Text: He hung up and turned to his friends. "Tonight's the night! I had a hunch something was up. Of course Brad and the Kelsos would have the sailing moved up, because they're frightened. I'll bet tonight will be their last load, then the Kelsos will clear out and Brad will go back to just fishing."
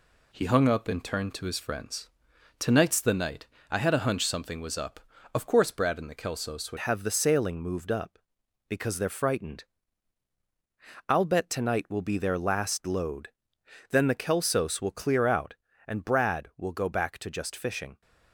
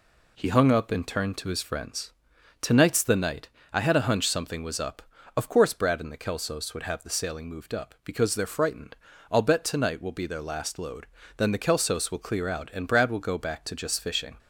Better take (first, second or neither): second